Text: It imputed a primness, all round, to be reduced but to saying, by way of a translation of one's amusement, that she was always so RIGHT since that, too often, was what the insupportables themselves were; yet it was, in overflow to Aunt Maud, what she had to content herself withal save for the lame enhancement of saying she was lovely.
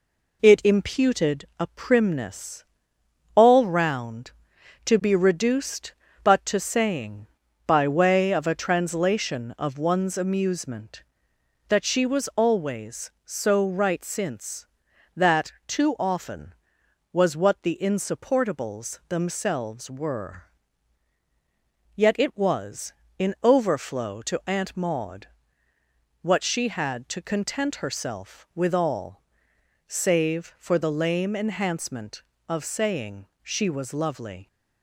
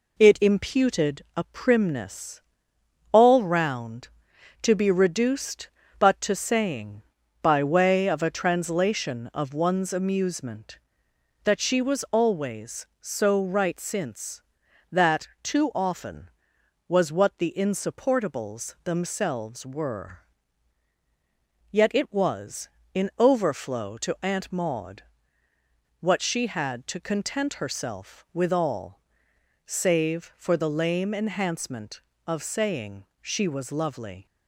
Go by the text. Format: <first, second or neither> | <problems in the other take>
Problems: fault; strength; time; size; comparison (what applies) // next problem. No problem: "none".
neither | pauses between "withal" and "save"; noticeable; the same in both // pauses between "saying" and "she"; slight; the same in both